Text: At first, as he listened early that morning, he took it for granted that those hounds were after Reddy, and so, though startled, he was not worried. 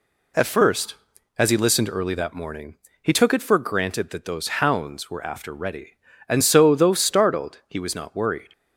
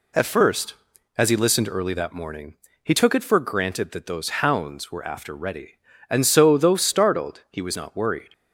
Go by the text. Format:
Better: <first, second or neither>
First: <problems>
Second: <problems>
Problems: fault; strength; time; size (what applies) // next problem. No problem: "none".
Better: neither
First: none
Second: none